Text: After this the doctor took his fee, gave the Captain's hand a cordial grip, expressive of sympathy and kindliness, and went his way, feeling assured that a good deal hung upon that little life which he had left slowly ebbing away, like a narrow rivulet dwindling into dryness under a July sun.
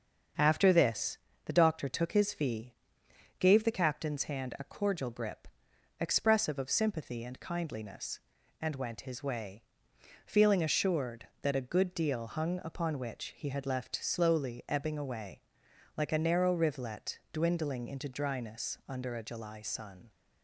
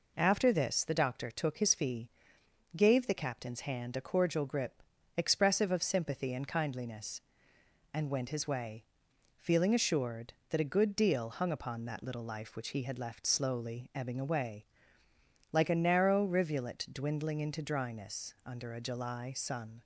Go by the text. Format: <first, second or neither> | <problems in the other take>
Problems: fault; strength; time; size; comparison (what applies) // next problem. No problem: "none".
second | starts louder than the rest; until 1.6 s; 7 dB // pauses between "this" and "the"; slight; at 1.1 s; 0.30 s long // skips "that little life"; at 12.9 s